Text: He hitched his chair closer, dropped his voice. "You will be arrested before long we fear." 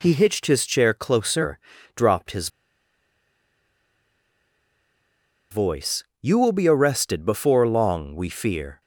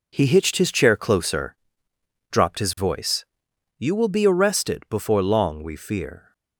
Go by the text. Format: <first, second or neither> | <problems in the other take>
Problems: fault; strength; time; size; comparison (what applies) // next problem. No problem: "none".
second | pauses between "his" and "voice"; strong; at 2.4 s; 3.0 s long